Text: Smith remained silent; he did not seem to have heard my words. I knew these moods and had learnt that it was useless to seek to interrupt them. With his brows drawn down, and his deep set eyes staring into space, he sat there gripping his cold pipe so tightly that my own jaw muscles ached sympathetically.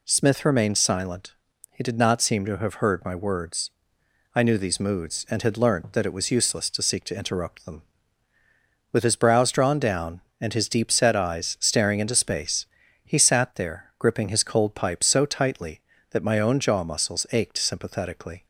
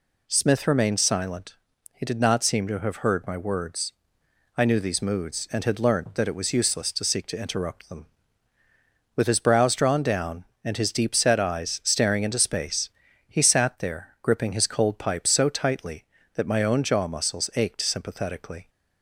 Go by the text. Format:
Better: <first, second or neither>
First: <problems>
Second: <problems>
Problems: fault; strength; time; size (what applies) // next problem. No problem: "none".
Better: neither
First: none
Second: none